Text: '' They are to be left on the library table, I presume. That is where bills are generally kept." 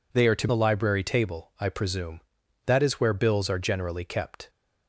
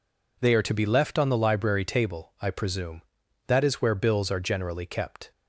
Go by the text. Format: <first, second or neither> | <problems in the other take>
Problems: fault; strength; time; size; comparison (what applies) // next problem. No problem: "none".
second | skips "be left on"; at 0.4 s